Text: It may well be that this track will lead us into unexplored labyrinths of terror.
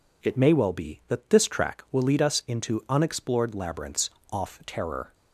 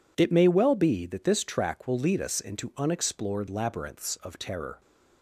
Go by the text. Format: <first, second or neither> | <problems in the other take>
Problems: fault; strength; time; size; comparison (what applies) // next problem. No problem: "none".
second | says "off" for "of"; at 4.3 s